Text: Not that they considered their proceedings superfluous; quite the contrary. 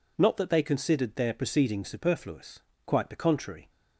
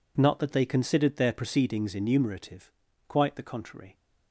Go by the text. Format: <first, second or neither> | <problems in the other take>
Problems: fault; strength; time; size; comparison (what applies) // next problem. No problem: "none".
first | says "enumerative" for "superfluous"; at 1.9 s